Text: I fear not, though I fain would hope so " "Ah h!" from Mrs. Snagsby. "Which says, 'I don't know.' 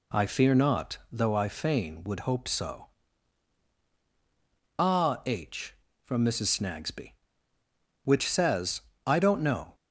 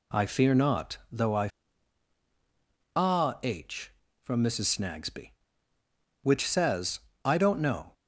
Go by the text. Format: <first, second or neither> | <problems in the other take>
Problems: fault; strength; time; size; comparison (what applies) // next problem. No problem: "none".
first | skips "fain would hope so"; at 1.7 s